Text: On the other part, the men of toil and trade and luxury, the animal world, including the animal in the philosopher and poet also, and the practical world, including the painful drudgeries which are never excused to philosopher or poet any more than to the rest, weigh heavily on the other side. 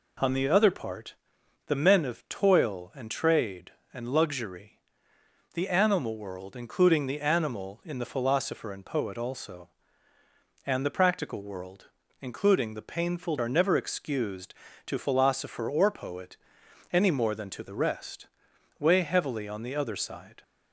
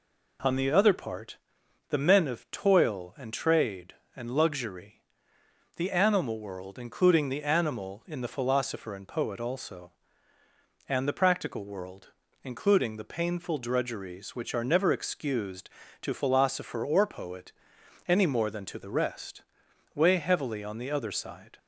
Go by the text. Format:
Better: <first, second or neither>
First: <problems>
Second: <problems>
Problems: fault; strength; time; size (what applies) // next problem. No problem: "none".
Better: second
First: skips "drudgeries which"; at 13.3 s // pauses between "poet" and "any"; noticeable; at 16.3 s; 0.56 s long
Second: pauses between "poet" and "any"; noticeable; at 17.5 s; 0.56 s long